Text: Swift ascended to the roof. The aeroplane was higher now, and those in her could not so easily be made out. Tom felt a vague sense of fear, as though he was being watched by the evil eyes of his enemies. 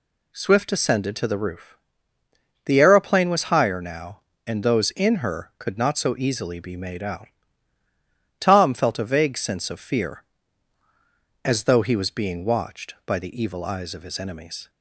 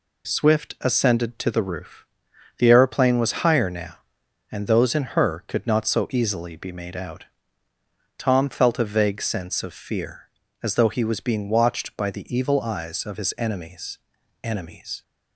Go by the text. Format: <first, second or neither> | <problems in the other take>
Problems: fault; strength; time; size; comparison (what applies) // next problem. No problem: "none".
first | says "enemies" twice; at 14.4 s